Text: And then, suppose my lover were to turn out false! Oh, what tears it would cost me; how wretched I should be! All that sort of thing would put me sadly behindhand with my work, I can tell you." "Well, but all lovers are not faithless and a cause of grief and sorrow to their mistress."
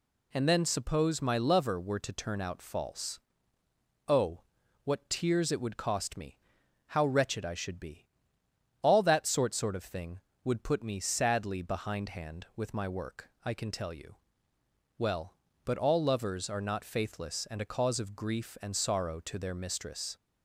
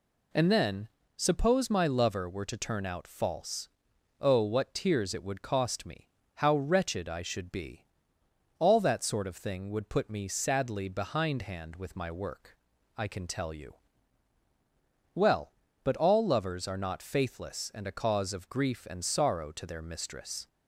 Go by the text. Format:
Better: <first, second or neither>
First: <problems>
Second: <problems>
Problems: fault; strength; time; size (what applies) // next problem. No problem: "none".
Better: second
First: says "sort" twice; at 9.5 s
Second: none